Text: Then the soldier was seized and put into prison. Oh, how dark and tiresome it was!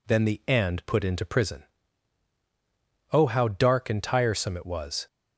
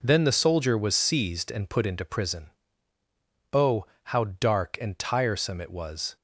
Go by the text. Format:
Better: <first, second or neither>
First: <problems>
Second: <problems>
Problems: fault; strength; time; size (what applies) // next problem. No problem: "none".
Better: second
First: skips "soldier was seized"; at 0.4 s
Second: none